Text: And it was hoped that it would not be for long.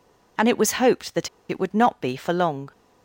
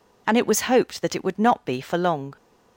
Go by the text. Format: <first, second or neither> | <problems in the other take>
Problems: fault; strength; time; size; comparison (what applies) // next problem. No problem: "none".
second | pauses between "that" and "it"; slight; at 1.2 s; 0.21 s long